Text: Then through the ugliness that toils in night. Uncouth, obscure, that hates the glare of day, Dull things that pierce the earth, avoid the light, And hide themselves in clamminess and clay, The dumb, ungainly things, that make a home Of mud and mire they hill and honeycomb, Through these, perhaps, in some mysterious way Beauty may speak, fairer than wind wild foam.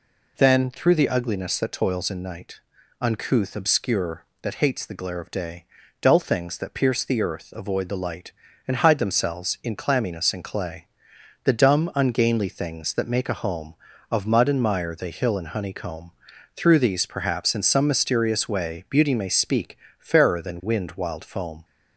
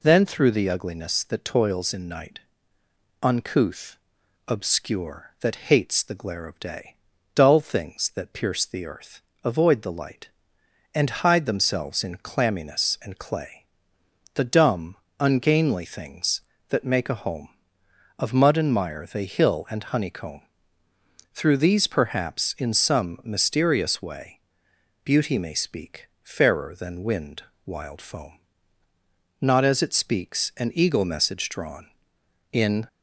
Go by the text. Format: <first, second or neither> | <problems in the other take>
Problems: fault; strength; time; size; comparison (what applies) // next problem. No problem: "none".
first | pauses between "way" and "Beauty"; noticeable; at 24.3 s; 0.66 s long // pauses between "wind" and "wild"; slight; at 27.4 s; 0.22 s long // goes on to say "Not as it speaks an eagle message drawn In"; strong; from 29.3 s on; 3.4 s long